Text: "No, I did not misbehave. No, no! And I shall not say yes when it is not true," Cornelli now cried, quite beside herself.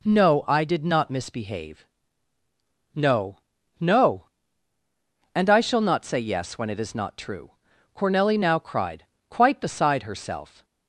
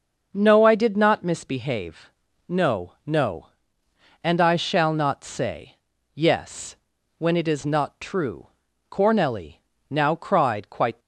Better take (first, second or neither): first